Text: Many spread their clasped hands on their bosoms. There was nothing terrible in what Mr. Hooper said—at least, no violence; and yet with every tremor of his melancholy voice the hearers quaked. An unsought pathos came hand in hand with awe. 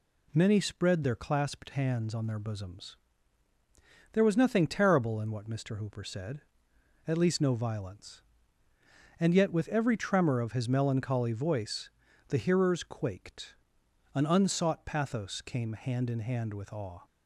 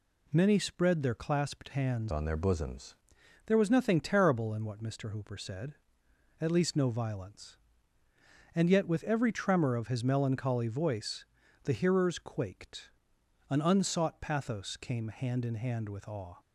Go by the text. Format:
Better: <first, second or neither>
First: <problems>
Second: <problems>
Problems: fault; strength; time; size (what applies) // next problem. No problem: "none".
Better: first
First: pauses between "voice" and "the"; at 11.8 s; 0.38 s long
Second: changes voice from "on" to "bosoms"; from 2.0 to 2.9 s; 0.9 s long // pauses between "voice" and "the"; at 11.2 s; 0.38 s long